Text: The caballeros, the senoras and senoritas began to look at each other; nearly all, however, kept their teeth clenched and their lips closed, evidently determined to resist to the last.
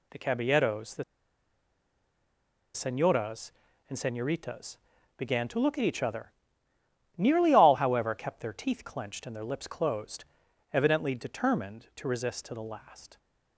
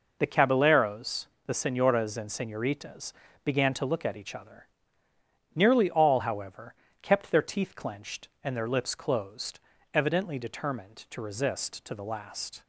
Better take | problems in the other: second | pauses between "the" and "senoras"; strong; at 1.0 s; 1.7 s long // pauses between "senoritas" and "began"; at 4.7 s; 0.40 s long; slight in the second

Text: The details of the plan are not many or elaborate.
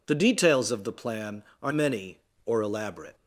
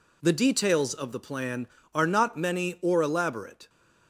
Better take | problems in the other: second | skips "not"; at 1.7 s

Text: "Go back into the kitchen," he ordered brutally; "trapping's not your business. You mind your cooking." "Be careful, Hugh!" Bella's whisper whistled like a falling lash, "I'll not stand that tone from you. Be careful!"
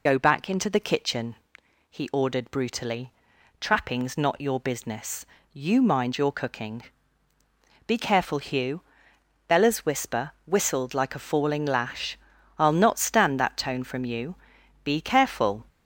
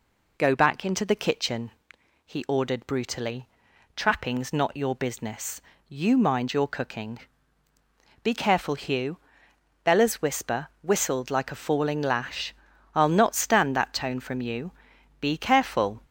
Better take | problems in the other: second | loses the start of "Go"; at 0.0 s; 30 ms

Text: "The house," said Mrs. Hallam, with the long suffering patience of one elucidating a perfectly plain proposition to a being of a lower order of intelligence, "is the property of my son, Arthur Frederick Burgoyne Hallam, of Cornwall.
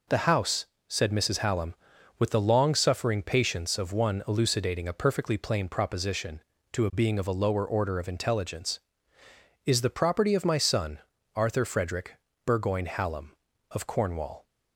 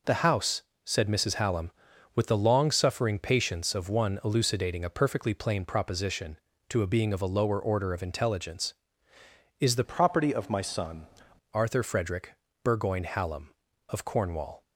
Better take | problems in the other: first | changes voice from "property" to "son"; from 9.8 to 11.0 s; 1.2 s long // pauses between "Frederick" and "Burgoyne"; slight; at 12.3 s; 0.28 s long; slight in the first

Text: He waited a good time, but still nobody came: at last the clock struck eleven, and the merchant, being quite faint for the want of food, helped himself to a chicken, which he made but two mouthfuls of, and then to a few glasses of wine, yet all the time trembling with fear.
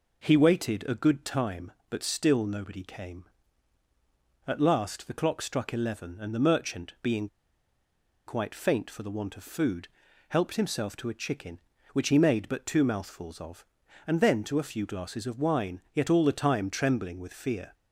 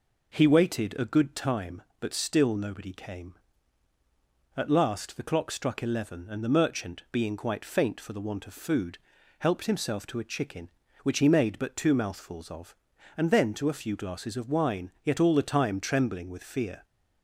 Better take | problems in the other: second | pauses between "being" and "quite"; at 7.2 s; 1.0 s long

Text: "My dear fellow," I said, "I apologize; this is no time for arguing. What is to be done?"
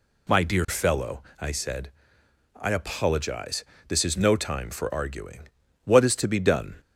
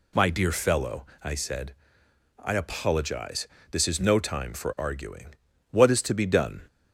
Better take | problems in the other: neither | none

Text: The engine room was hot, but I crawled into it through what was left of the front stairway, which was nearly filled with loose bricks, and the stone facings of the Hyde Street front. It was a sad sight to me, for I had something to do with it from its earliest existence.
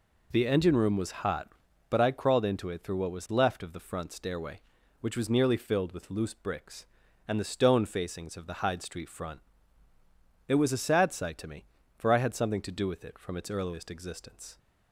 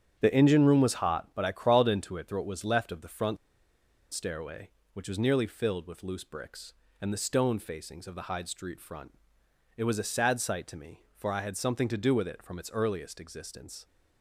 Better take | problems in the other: first | starts louder than the rest; strong; until 1.2 s; 9 dB // pauses between "front" and "stairway"; noticeable; at 3.3 s; 0.76 s long

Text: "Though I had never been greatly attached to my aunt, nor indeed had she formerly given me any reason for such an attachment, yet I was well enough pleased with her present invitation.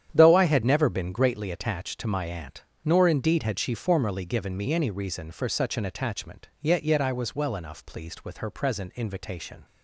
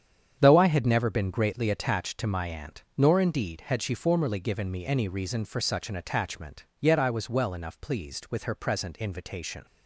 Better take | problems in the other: second | starts louder than the rest; strong; until 1.1 s; 9.5 dB; strong in the second // says "yet" twice; at 6.8 s

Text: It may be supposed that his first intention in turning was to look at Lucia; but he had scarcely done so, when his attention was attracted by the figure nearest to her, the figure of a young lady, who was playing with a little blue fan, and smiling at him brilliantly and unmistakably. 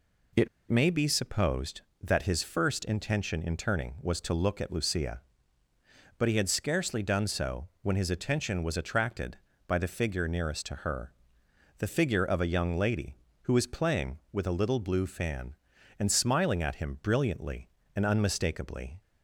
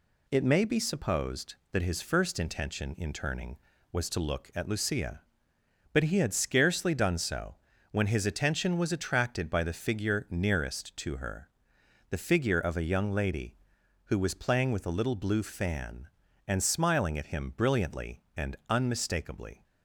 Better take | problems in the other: second | pauses between "It" and "may"; slight; at 0.4 s; 0.22 s long

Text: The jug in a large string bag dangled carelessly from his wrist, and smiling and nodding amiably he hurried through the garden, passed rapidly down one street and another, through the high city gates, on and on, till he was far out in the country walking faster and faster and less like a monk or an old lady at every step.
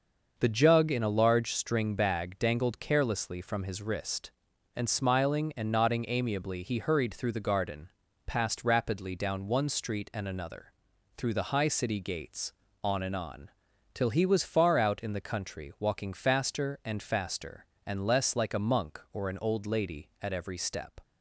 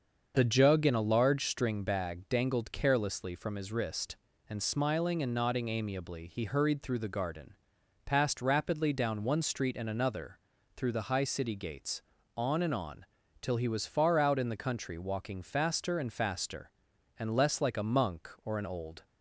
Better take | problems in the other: first | starts louder than the rest; until 1.3 s; 6.5 dB; noticeable in the first // stops before "lady at every step"; at 19.0 s

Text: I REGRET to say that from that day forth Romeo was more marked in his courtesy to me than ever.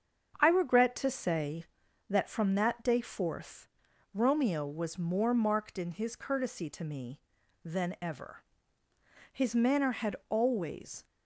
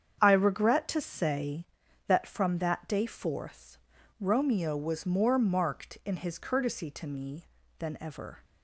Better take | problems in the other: second | starts louder than the rest; strong; until 1.4 s; 7.5 dB; strong in the second // pauses between "forth" and "Romeo"; at 3.6 s; 0.44 s long; also in the second // goes on to say "His manner had always"; strong; from 9.3 s on; 1.7 s long

